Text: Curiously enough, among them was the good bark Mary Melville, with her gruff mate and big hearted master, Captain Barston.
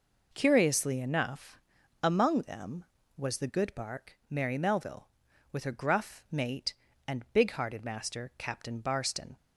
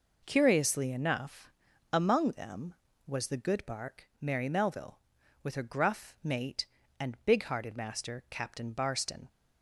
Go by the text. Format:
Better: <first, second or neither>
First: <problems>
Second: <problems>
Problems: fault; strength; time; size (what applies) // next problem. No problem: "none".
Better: neither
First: none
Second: none